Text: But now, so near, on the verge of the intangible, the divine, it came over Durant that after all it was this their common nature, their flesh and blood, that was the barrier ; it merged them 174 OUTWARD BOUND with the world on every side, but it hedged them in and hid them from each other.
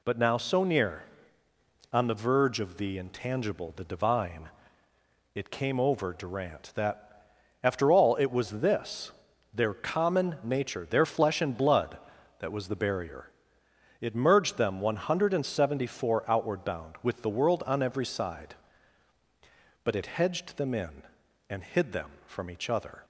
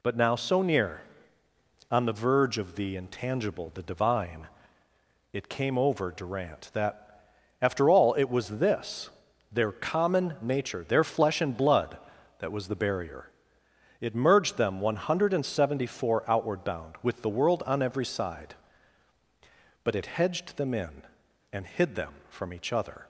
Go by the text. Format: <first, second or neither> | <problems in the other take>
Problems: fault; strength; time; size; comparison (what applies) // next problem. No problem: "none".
neither | pauses between "that" and "after"; slight; the same in both // pauses between "this" and "their"; the same in both